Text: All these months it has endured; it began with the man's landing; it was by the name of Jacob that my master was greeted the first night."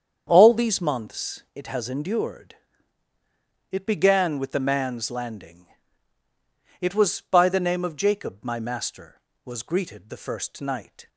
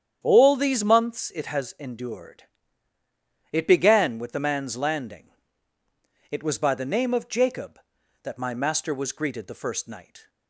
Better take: second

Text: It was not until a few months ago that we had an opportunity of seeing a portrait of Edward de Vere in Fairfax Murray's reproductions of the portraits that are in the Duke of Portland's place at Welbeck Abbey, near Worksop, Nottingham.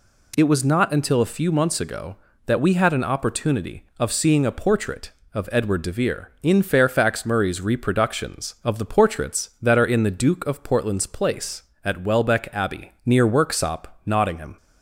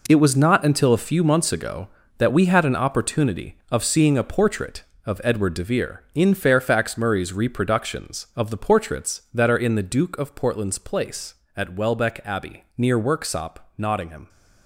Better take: first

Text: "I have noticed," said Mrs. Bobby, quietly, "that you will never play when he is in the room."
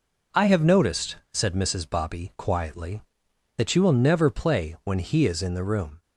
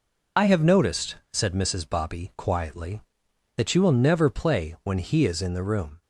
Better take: first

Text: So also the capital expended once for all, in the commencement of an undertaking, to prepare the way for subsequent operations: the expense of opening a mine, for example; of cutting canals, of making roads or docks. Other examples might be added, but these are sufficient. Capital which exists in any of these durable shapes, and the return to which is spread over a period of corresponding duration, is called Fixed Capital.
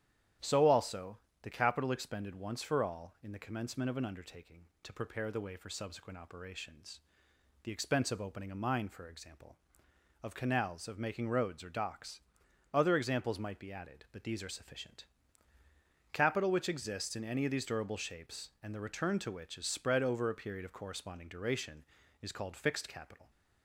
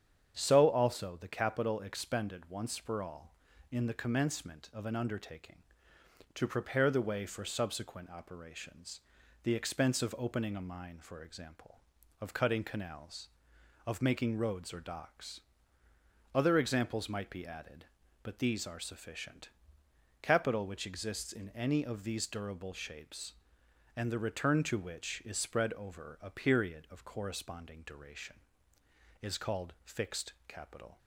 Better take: second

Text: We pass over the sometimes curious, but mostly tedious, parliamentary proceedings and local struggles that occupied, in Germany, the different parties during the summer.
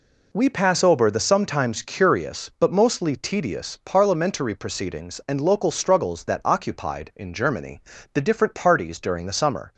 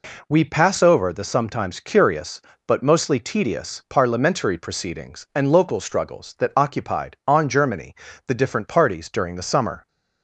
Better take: first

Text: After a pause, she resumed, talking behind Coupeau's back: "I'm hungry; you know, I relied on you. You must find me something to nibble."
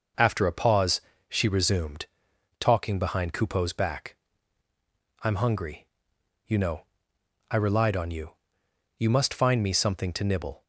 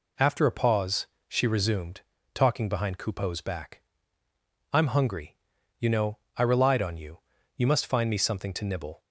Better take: neither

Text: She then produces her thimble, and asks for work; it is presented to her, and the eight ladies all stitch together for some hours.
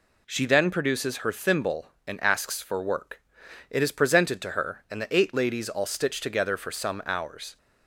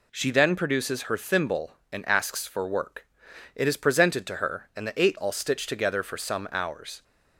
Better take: first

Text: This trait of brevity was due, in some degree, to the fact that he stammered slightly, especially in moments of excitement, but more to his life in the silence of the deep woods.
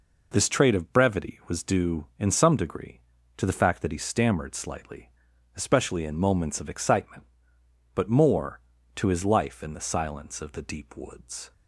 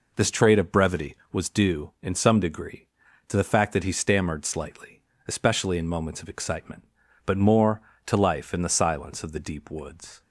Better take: first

